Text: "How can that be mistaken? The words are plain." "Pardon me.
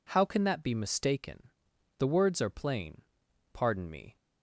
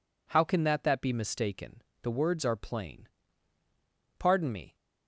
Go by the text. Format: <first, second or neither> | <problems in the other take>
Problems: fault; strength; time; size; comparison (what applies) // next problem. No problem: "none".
first | says "that" twice; at 0.8 s